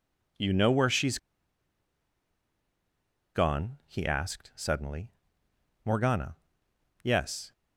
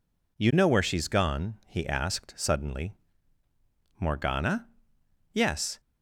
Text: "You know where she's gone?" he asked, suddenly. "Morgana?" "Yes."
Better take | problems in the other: second | pauses between "she's" and "gone"; strong; at 1.1 s; 2.1 s long

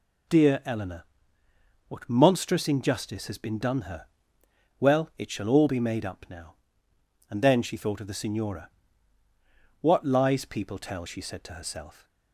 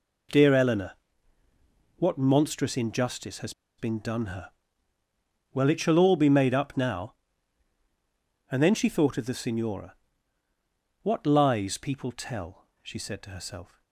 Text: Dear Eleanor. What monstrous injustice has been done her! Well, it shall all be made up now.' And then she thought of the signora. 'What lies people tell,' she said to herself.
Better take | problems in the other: first | pauses between "has" and "been"; slight; at 3.5 s; 0.26 s long

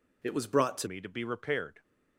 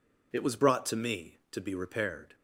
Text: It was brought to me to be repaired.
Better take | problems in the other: second | changes voice at "me"; from 0.8 s on; 1.0 s long

